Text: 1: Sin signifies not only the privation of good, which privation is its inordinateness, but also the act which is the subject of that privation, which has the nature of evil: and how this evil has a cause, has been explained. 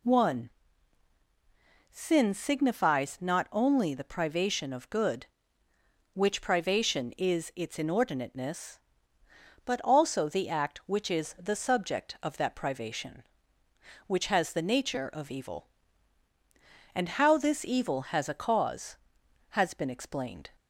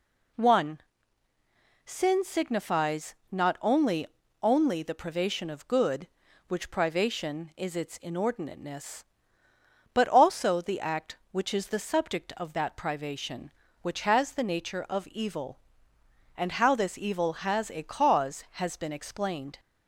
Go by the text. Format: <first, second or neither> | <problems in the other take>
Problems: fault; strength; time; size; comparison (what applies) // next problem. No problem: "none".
first | pauses between "signifies" and "not"; slight; at 3.1 s; 0.16 s long // says "only" twice; at 4.4 s